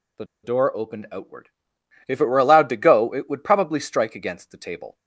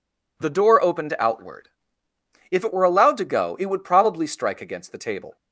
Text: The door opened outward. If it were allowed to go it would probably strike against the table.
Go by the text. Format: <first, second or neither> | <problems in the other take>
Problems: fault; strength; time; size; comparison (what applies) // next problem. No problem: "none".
second | pauses between "The" and "door"; slight; at 0.2 s; 0.18 s long